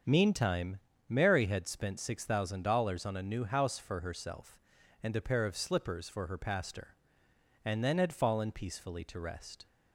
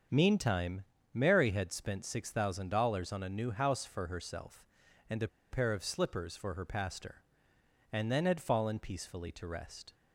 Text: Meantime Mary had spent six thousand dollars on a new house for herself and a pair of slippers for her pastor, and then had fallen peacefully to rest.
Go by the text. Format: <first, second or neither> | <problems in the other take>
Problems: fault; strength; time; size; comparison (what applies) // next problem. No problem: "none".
first | starts louder than the rest; until 1.4 s; 7 dB; also in the first // pauses between "Meantime" and "Mary"; slight; at 0.8 s; 0.30 s long; slight in the first // pauses between "a" and "pair"; slight; at 5.2 s; 0.23 s long